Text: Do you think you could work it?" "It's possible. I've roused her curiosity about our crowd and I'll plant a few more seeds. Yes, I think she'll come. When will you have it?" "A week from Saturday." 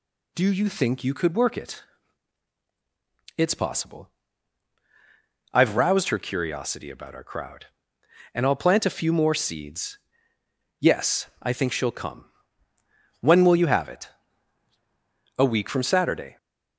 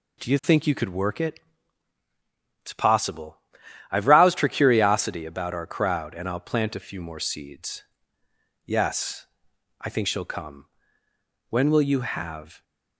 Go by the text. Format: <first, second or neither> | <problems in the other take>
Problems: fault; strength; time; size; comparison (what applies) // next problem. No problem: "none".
first | stops before "it A week from Saturday"; at 12.6 s